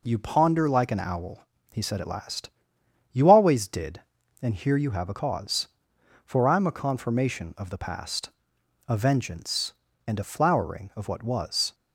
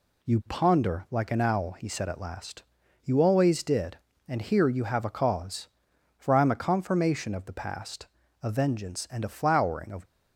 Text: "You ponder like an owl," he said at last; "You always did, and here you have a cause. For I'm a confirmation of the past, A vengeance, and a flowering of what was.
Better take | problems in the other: first | stops before "what was"; at 10.0 s

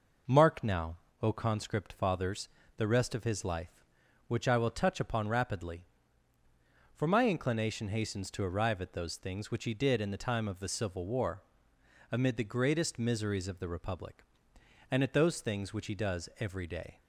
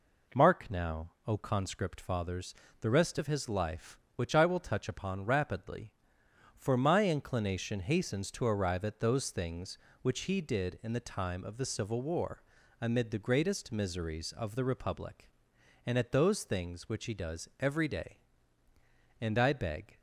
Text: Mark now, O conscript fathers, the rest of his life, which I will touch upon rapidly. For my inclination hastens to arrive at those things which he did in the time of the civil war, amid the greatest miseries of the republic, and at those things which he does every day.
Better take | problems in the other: first | goes on to say "And I beg"; noticeable; from 19.1 s on; 0.80 s long

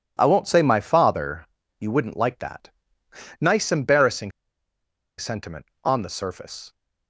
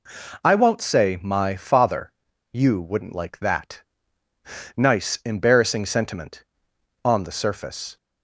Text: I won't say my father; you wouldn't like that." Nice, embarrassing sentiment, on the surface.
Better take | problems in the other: second | pauses between "embarrassing" and "sentiment"; noticeable; at 4.3 s; 0.87 s long

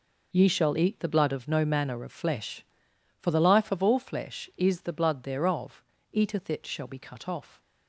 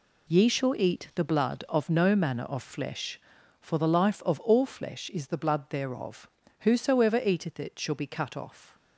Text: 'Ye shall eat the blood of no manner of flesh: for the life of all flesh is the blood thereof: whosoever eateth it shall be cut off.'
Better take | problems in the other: second | skips "whosoever"; at 5.9 s

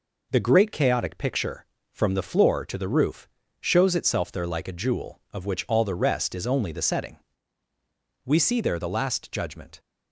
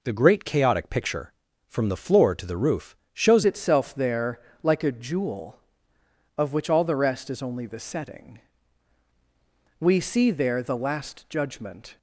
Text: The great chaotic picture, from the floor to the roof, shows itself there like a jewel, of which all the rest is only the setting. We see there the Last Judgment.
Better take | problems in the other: first | changes voice at "itself"; from 3.4 s on; 8.5 s long // pauses between "there" and "like"; slight; at 4.3 s; 0.24 s long

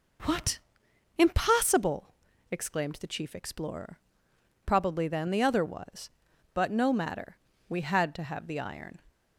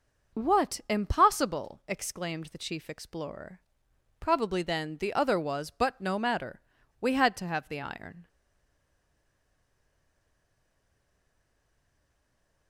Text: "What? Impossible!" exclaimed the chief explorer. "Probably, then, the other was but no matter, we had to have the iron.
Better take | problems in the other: first | stays silent after the last word; strong; from 8.2 s on; 4.4 s long

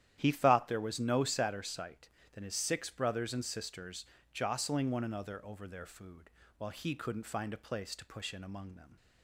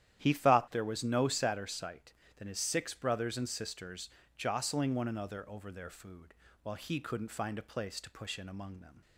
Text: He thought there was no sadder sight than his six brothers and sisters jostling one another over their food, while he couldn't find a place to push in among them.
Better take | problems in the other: neither | starts louder than the rest; strong; the same in both // pauses between "sisters" and "jostling"; slight; the same in both

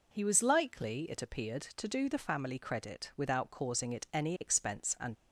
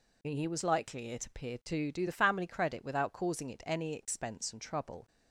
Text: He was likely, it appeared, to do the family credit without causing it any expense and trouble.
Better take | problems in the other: second | stops before "trouble"; at 5.1 s

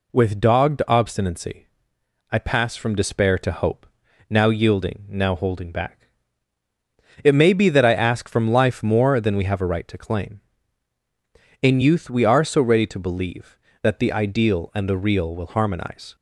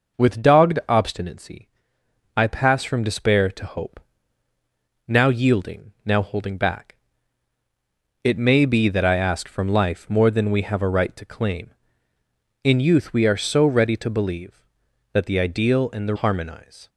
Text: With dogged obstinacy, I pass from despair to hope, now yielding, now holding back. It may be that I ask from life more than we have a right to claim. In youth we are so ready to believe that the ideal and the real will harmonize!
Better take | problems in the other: first | skips "real will"; at 16.1 s

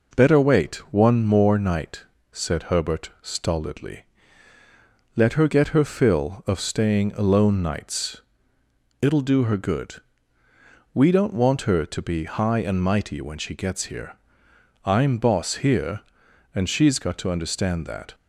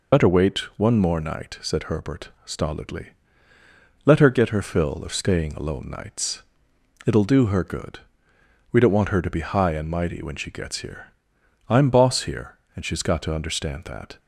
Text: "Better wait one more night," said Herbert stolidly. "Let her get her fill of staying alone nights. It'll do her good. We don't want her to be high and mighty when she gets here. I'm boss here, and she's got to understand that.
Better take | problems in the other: first | loses the start of "Better"; at 0.1 s; 95 ms // pauses between "wait" and "one"; slight; at 0.5 s; 0.20 s long; slight in the first // pauses between "Herbert" and "stolidly"; slight; at 2.2 s; 0.16 s long

